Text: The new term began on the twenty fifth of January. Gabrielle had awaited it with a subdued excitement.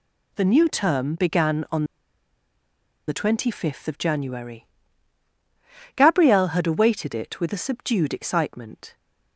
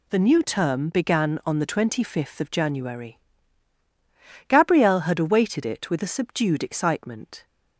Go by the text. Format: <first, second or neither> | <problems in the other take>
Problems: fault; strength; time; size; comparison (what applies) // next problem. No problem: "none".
second | pauses between "on" and "the"; at 1.8 s; 1.2 s long